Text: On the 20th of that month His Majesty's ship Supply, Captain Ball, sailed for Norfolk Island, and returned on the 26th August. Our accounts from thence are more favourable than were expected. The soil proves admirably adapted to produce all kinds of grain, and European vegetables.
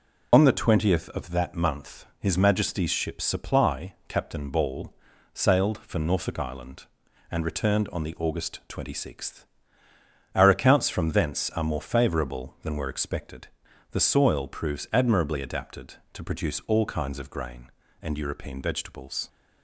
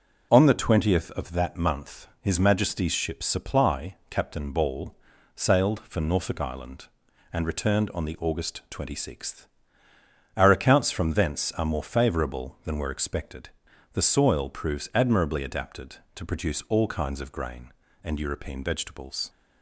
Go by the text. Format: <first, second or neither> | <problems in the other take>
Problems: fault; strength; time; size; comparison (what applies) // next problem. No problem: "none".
second | loses the start of "On"; at 0.3 s; 35 ms